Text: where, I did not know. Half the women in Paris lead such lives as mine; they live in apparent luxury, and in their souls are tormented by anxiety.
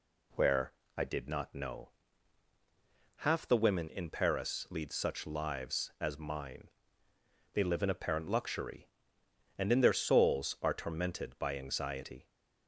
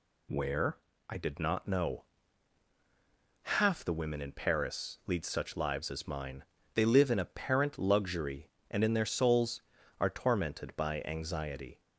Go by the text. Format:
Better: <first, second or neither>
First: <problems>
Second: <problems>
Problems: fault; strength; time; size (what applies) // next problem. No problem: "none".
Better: neither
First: none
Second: none